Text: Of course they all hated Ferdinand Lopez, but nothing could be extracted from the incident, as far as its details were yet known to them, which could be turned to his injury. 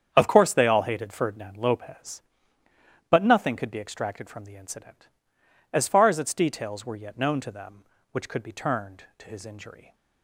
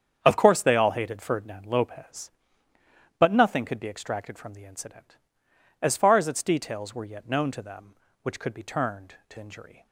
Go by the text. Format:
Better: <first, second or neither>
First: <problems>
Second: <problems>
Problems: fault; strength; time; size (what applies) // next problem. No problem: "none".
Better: first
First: starts louder than the rest; strong; until 1.1 s; 8 dB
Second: starts louder than the rest; strong; until 1.2 s; 8 dB // skips "his"; at 9.3 s